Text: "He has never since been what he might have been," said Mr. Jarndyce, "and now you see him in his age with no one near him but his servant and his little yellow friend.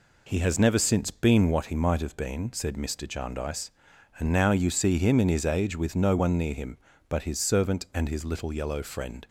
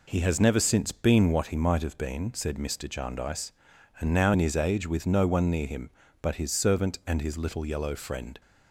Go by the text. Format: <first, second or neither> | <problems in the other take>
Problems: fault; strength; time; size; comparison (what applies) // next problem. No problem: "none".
first | skips "you see him"; at 4.3 s